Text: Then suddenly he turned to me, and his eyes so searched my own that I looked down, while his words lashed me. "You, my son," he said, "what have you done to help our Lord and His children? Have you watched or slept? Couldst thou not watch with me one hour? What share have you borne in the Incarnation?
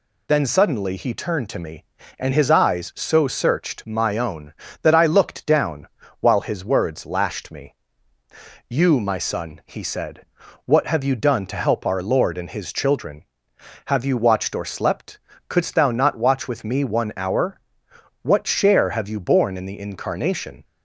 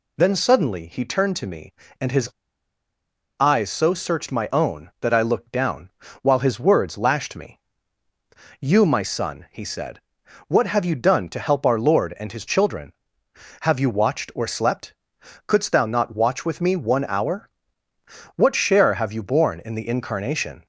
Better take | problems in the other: first | pauses between "his" and "eyes"; at 2.2 s; 1.1 s long

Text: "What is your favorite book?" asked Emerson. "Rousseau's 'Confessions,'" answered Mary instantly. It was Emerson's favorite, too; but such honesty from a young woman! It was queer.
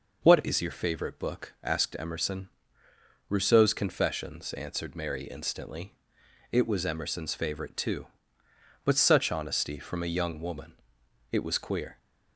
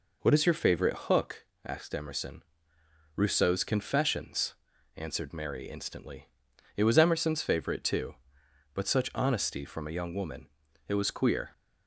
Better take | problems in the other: first | says "hook" for "book"; at 1.0 s

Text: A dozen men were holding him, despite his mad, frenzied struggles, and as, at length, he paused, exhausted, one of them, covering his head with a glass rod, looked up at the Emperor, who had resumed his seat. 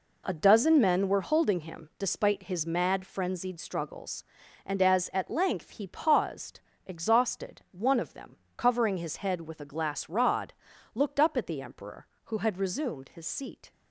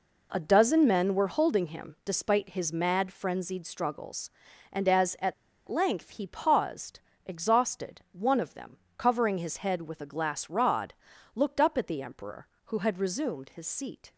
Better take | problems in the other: first | pauses between "at" and "length"; slight; at 5.3 s; 0.34 s long

